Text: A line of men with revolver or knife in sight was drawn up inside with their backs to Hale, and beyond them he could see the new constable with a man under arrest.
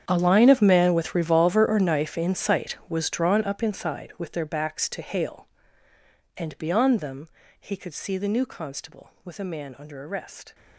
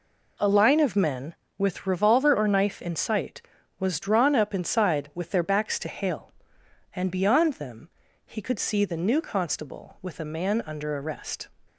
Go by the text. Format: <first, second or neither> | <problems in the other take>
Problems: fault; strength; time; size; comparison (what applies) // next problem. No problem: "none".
second | gets quieter; strong; throughout; 18 dB // pauses between "them" and "he"; slight; at 7.2 s; 0.32 s long; also in the second